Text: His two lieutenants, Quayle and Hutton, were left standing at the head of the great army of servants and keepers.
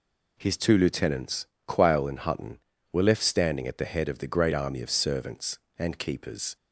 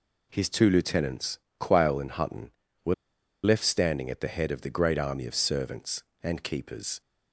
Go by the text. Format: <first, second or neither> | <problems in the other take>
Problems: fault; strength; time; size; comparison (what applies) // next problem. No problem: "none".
first | pauses between "were" and "left"; noticeable; at 2.9 s; 0.50 s long